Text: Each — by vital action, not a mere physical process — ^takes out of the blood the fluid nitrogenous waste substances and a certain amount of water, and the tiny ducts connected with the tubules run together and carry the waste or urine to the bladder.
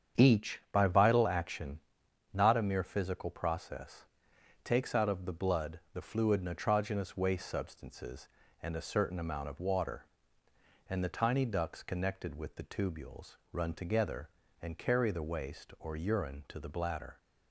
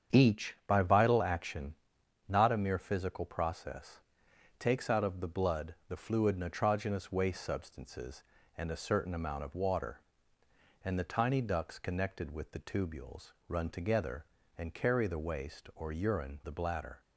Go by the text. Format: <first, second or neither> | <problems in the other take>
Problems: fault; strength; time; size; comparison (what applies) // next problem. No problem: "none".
first | starts louder than the rest; strong; until 1.2 s; 8 dB; strong in the first // pauses between "tubules" and "run"; slight; at 13.3 s; 0.16 s long; slight in the first // skips "to"; at 16.4 s